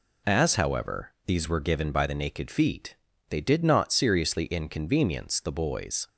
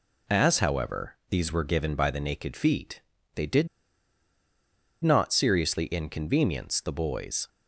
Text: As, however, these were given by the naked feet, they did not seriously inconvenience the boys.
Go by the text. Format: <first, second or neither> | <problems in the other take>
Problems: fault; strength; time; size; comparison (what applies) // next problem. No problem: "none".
first | pauses between "did" and "not"; strong; at 3.6 s; 1.3 s long